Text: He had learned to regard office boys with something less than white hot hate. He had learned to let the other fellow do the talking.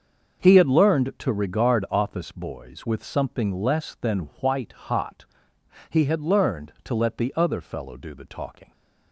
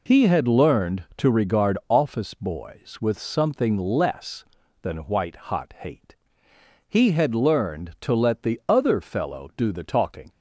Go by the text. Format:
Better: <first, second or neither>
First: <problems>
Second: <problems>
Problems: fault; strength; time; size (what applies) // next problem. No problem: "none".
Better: second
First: starts louder than the rest; until 1.4 s; 6.5 dB // skips "hate"; at 5.5 s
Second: none